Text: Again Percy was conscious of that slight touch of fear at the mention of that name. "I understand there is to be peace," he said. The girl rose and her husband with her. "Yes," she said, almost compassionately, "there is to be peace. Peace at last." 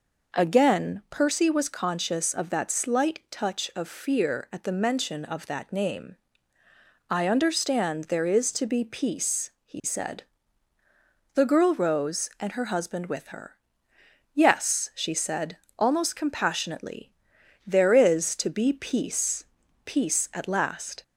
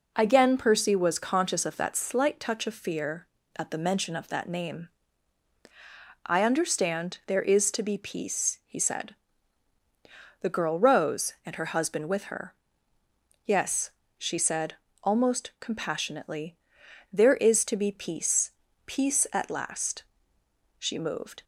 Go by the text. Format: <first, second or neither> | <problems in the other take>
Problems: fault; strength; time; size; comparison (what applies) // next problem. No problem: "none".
first | goes on to say "She moved"; noticeable; from 20.7 s on; 0.66 s long